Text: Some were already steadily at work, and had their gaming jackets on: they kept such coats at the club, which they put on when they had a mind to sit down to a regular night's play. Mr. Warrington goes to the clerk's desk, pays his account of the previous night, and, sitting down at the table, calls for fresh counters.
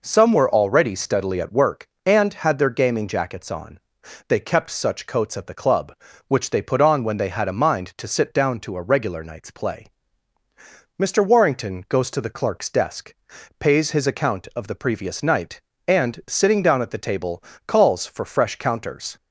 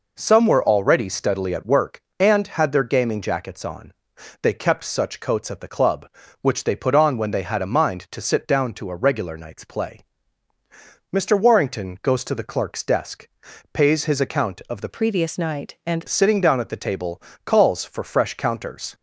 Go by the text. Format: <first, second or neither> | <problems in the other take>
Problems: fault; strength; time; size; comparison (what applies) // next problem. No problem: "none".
first | changes voice from "previous" to "and"; from 14.8 to 16.0 s; 1.2 s long